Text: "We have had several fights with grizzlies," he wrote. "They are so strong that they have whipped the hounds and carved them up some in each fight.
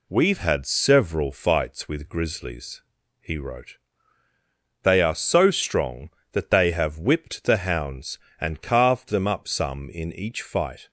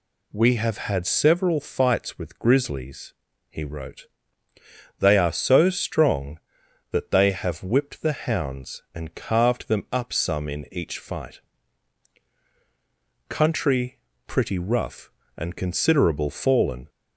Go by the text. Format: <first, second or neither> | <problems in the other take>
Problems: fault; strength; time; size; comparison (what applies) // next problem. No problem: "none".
first | goes on to say "Country pretty rough and considerable fallen"; strong; from 13.2 s on; 3.6 s long